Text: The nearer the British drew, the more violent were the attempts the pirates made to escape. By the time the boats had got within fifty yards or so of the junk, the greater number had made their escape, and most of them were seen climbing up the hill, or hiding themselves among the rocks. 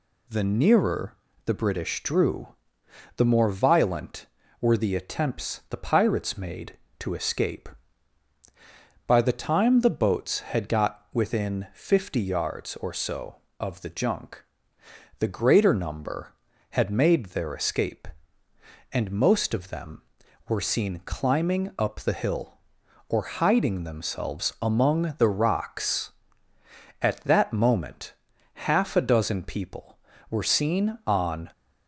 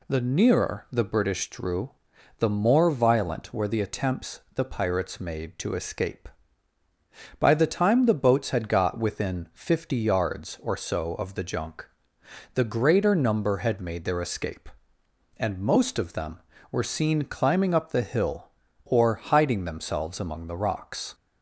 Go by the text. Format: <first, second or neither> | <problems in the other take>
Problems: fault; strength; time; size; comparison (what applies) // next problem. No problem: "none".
second | pauses between "nearer" and "the"; slight; at 1.1 s; 0.32 s long // goes on to say "At that moment half a dozen people were seen on"; strong; from 26.9 s on; 4.5 s long